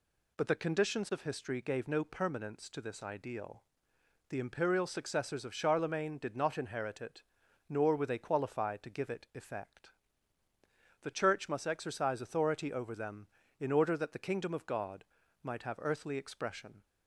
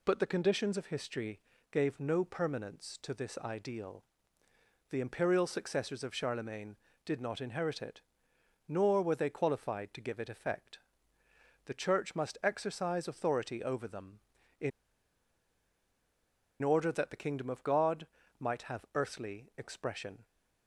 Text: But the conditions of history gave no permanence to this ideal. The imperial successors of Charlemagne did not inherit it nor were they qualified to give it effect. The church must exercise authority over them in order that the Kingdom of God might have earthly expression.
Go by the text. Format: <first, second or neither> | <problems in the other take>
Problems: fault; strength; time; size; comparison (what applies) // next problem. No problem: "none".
first | pauses between "history" and "gave"; slight; at 1.3 s; 0.32 s long // pauses between "it" and "nor"; noticeable; at 8.0 s; 0.64 s long; noticeable in the first // pauses between "in" and "order"; strong; at 14.7 s; 1.9 s long // pauses between "God" and "might"; slight; at 18.0 s; 0.34 s long; also in the first